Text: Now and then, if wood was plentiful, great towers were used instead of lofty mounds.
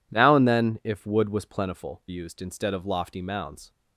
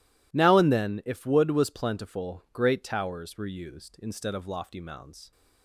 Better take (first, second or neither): second